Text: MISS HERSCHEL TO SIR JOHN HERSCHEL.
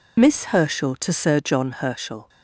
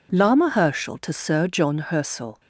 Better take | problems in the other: first | says "Lama" for "MISS"; at 0.1 s

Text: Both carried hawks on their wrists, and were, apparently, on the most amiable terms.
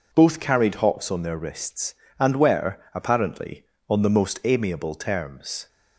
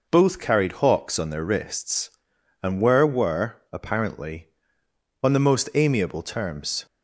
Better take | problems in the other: first | says "were" twice; at 3.0 s

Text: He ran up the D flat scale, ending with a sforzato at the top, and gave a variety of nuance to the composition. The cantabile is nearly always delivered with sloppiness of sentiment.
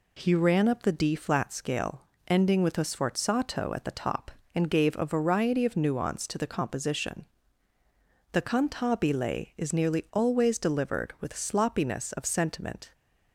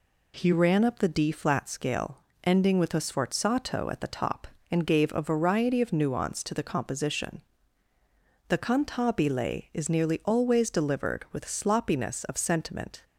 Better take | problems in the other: neither | none

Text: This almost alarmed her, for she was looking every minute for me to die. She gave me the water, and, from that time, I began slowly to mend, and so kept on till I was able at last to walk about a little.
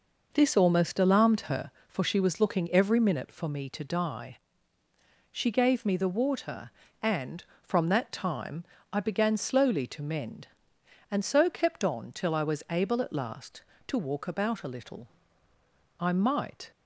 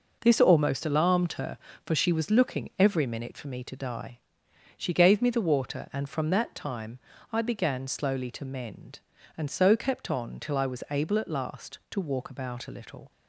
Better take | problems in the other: second | goes on to say "I might"; noticeable; from 15.9 s on; 0.72 s long

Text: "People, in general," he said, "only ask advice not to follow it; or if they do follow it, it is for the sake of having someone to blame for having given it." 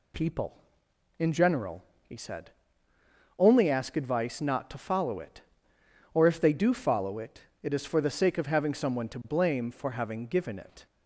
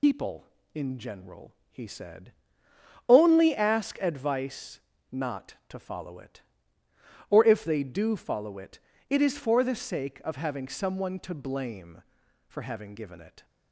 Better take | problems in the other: first | loses the start of "People"; at 0.0 s; 105 ms // pauses between "advice" and "not"; slight; at 4.7 s; 0.32 s long

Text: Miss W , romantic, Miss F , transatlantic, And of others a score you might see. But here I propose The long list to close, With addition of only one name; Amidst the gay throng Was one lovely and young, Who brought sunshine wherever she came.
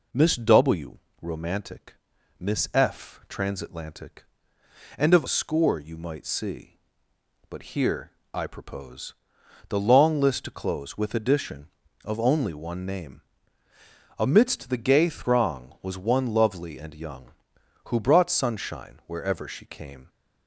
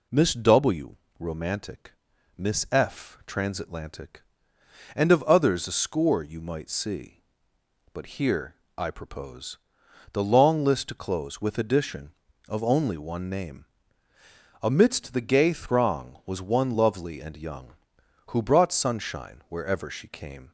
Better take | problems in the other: second | skips "others"; at 5.2 s // pauses between "here" and "I"; slight; at 8.1 s; 0.22 s long; slight in the second // pauses between "propose" and "The"; noticeable; at 9.1 s; 0.56 s long; noticeable in the second

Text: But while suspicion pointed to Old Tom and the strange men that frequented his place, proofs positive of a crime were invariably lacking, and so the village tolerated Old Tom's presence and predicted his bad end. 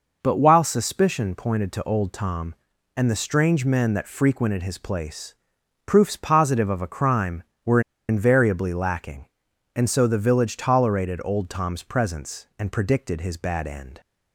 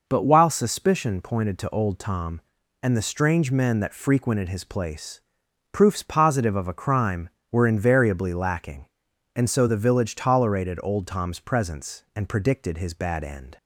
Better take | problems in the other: second | pauses between "were" and "invariably"; slight; at 7.7 s; 0.28 s long

